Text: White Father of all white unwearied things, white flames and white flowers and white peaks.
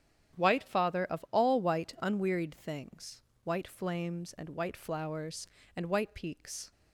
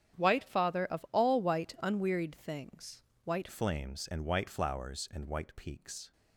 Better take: first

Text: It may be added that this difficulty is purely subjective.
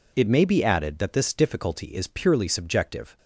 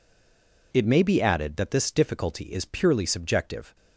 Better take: first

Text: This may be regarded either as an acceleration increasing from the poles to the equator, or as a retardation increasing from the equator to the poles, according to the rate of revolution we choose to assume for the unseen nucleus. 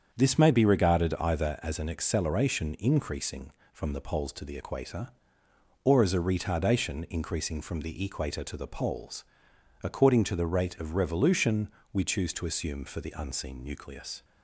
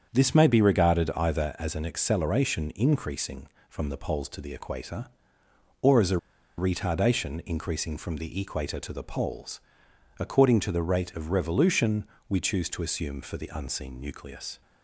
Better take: first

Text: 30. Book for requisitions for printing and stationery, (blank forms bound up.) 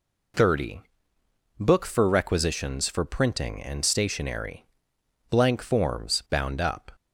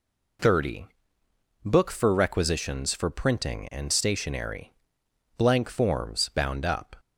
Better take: neither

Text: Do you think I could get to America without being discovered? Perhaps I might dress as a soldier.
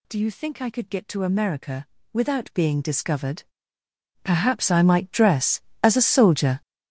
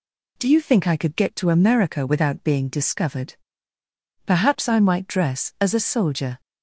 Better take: second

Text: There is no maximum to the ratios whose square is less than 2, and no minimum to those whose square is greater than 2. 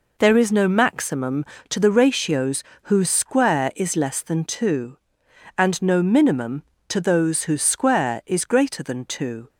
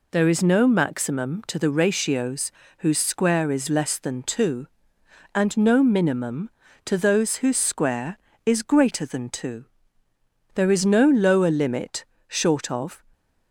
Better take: first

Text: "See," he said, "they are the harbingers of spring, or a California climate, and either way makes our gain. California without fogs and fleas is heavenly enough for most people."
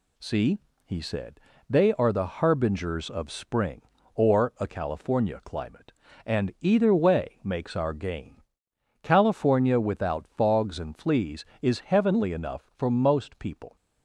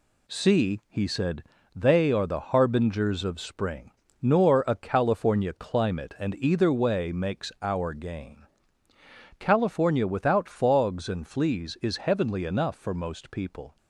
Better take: first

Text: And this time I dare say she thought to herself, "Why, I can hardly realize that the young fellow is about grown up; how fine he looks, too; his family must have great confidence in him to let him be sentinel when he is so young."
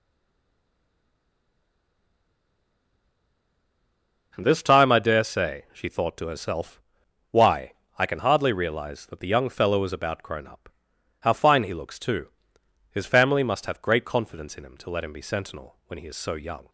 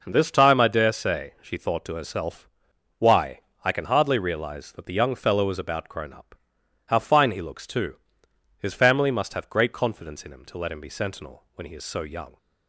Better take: second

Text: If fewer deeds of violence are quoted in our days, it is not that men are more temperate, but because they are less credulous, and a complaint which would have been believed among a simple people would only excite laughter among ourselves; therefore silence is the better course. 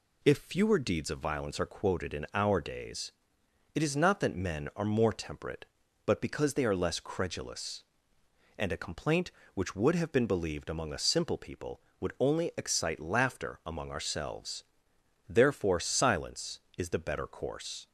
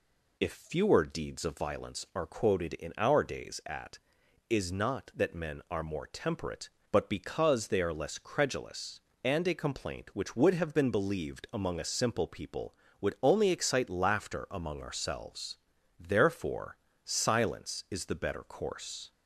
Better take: first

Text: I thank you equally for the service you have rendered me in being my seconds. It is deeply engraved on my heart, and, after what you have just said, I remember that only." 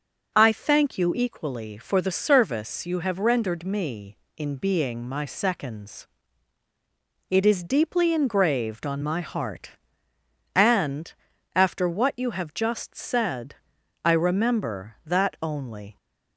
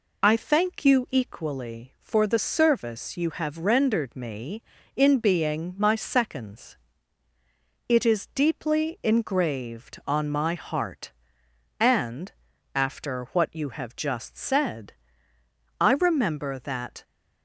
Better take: first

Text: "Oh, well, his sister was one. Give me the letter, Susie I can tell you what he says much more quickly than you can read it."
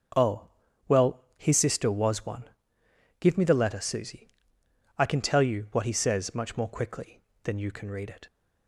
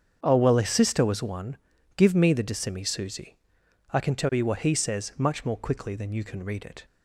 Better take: first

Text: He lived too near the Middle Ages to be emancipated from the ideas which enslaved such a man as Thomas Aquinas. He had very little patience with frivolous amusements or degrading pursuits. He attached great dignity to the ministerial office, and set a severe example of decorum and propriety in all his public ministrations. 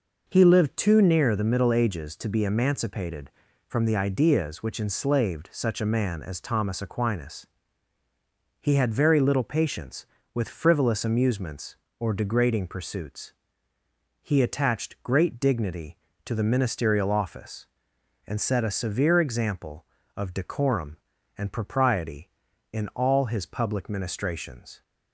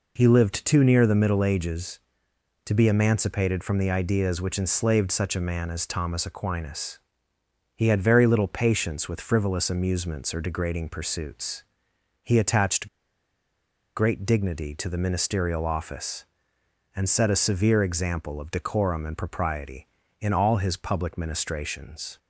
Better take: first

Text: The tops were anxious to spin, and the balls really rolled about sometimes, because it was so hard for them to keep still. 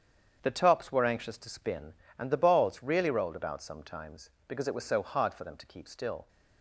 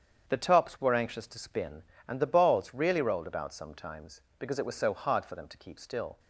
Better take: neither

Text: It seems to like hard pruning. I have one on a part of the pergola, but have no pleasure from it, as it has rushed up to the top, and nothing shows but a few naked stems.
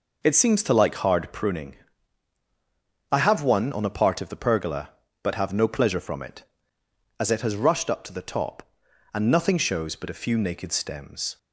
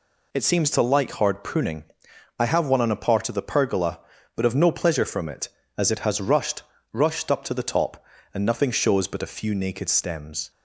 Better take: first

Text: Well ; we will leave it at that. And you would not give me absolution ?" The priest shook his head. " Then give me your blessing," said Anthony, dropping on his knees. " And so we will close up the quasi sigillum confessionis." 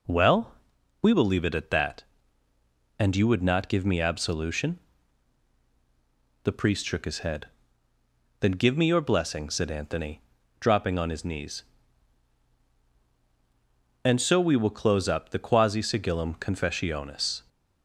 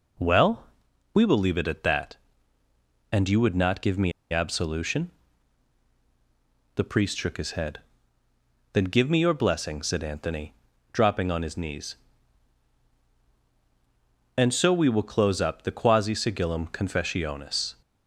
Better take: first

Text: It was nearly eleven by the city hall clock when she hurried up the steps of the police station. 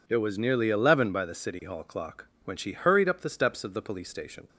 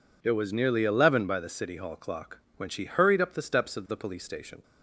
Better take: neither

